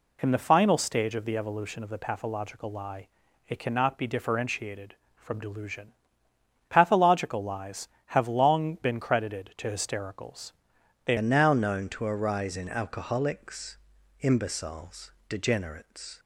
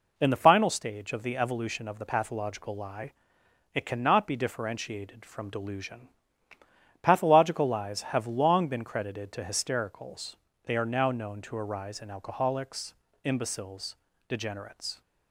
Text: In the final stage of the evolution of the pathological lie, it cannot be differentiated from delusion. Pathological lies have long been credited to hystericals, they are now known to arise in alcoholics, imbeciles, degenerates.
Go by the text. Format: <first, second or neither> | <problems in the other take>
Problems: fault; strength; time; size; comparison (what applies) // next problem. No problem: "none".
second | changes voice at "are"; from 11.1 s on; 5.0 s long